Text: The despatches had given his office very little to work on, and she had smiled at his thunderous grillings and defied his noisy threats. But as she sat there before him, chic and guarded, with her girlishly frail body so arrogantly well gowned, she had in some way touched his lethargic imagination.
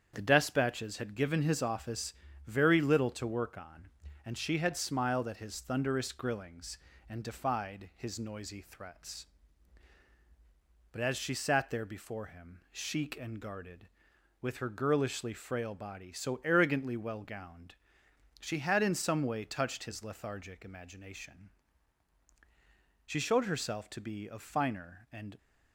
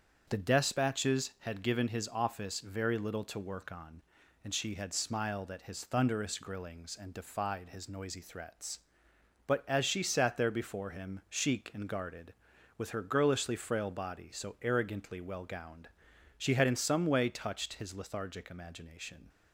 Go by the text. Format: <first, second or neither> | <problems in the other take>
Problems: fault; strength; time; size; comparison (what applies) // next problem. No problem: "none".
second | starts louder than the rest; strong; until 1.1 s; 8 dB; strong in the second // pauses between "office" and "very"; slight; at 2.1 s; 0.34 s long // goes on to say "She showed herself to be of finer and"; strong; from 23.0 s on; 2.3 s long